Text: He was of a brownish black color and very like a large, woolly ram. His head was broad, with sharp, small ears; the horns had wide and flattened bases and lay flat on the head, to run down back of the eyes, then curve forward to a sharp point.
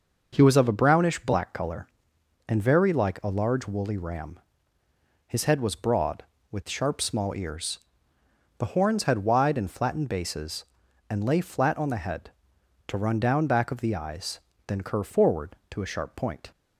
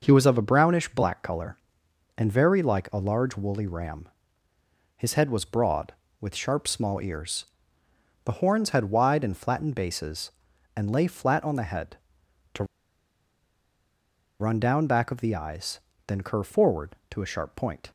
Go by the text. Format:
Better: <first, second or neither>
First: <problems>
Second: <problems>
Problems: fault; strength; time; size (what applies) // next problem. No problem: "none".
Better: first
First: none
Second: pauses between "to" and "run"; strong; at 12.6 s; 1.7 s long